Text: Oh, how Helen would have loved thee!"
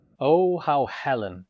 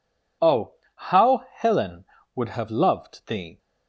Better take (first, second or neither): second